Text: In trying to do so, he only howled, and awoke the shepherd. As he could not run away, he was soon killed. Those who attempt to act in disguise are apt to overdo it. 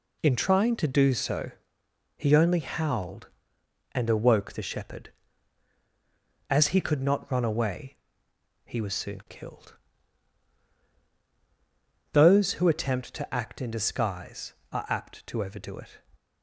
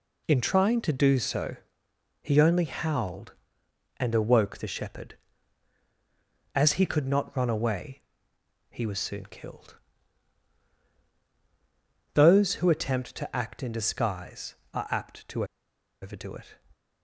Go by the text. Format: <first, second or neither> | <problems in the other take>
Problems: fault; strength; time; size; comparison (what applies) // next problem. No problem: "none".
first | pauses between "to" and "overdo"; noticeable; at 15.4 s; 0.56 s long